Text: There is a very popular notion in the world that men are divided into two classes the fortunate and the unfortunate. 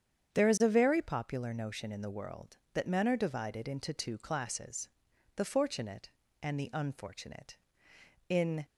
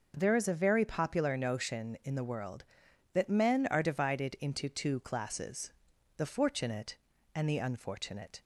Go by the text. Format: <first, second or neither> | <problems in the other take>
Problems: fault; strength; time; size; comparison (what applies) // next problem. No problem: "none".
second | starts louder than the rest; strong; until 1.3 s; 8 dB // pauses between "classes" and "the"; noticeable; at 4.8 s; 0.46 s long; noticeable in the second // goes on to say "In"; slight; from 8.2 s on; 0.36 s long